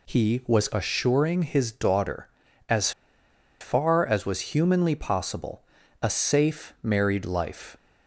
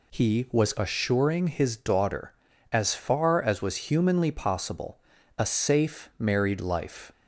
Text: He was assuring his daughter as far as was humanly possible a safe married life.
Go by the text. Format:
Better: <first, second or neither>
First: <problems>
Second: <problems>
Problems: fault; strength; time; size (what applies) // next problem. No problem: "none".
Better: second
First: pauses between "as" and "far"; noticeable; at 2.9 s; 0.69 s long // pauses between "possible" and "a"; at 5.6 s; 0.38 s long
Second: pauses between "possible" and "a"; at 4.9 s; 0.38 s long